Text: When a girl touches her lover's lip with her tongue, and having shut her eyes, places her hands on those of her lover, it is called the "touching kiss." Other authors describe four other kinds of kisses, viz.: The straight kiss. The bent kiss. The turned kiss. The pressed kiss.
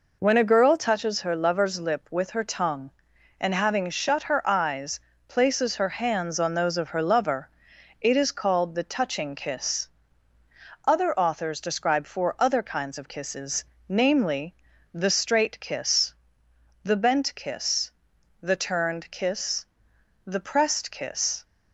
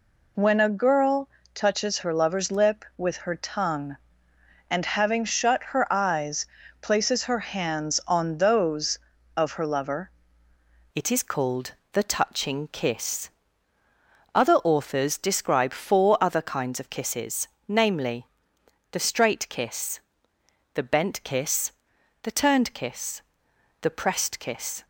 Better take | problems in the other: first | pauses between "girl" and "touches"; slight; at 1.2 s; 0.24 s long // changes voice at "it"; from 10.9 s on; 13.9 s long // pauses between "called" and "the"; slight; at 11.7 s; 0.18 s long

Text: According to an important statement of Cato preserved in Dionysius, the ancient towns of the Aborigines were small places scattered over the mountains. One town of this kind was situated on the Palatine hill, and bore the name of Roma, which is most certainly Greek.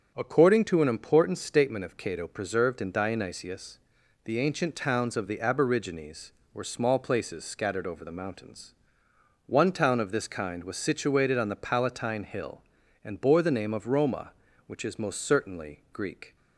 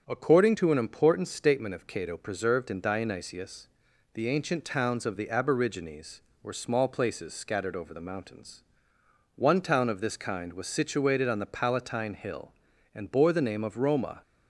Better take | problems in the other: first | starts louder than the rest; until 1.0 s; 7 dB; strong in the first // stops before "which is most certainly Greek"; at 14.2 s

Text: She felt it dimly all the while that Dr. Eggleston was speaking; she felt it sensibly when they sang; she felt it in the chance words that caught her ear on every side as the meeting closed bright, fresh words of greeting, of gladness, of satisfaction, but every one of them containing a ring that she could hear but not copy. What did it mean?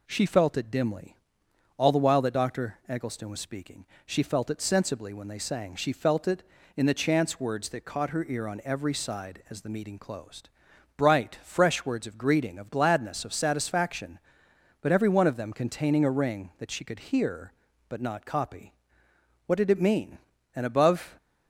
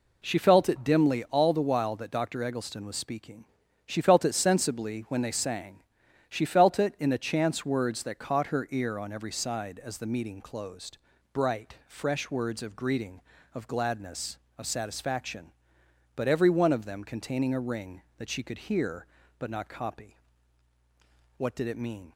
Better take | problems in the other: second | pauses between "dimly" and "all"; noticeable; at 1.1 s; 0.64 s long // pauses between "closed" and "bright"; noticeable; at 10.4 s; 0.46 s long; slight in the second // goes on to say "And above"; noticeable; from 20.5 s on; 0.62 s long

